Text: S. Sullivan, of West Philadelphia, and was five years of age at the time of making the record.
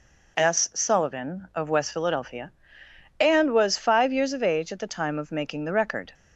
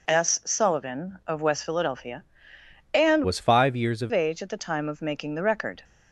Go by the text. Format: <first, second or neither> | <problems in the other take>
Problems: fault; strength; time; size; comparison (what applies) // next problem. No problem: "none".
first | changes voice from "was" to "of"; from 3.2 to 4.1 s; 0.9 s long